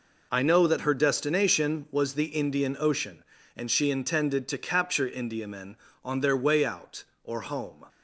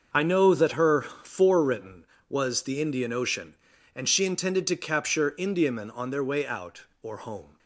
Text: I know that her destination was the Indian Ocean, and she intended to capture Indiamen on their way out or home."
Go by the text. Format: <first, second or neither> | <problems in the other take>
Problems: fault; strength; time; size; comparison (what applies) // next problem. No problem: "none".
first | starts louder than the rest; until 1.1 s; 6.5 dB // says "forewritten" for "destination"; at 1.0 s